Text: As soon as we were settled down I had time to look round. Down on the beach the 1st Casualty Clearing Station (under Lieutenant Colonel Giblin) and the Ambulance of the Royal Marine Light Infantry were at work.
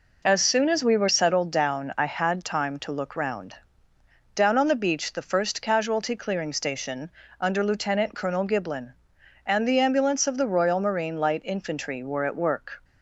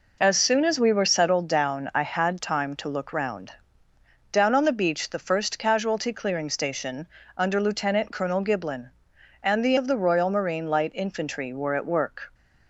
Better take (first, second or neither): first